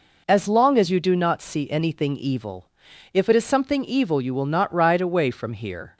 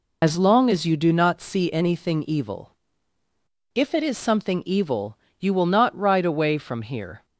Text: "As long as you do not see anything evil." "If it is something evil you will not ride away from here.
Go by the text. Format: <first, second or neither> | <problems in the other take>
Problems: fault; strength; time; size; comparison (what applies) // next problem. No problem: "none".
first | loses the start of "As"; at 0.2 s; 40 ms // pauses between "evil" and "you"; slight; at 5.1 s; 0.24 s long